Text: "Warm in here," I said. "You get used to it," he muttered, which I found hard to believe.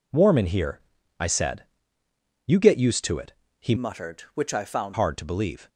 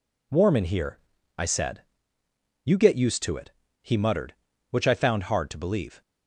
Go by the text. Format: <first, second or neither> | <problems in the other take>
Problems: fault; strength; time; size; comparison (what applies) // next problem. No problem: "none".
second | changes voice from "muttered" to "found"; from 3.7 to 4.9 s; 1.2 s long